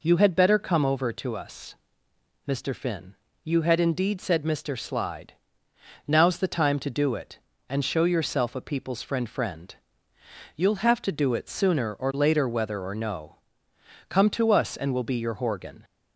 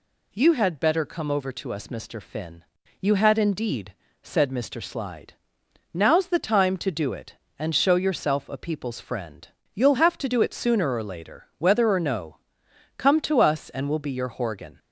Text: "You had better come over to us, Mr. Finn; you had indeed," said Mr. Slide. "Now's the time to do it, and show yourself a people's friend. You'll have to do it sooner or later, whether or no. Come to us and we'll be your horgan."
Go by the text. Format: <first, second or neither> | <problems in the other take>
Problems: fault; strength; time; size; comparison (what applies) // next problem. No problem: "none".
second | says "friend" twice; at 9.2 s